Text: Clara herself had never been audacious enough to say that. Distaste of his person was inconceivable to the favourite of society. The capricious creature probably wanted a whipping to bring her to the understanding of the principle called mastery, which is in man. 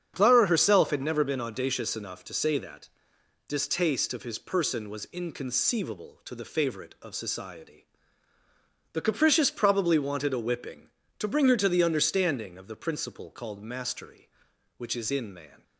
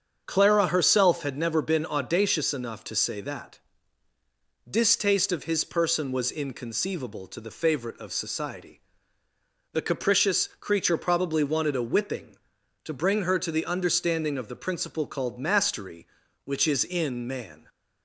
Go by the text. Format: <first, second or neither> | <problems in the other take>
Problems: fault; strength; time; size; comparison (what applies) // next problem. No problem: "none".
second | starts louder than the rest; strong; until 1.1 s; 8 dB; strong in the second // skips "creature"; at 9.5 s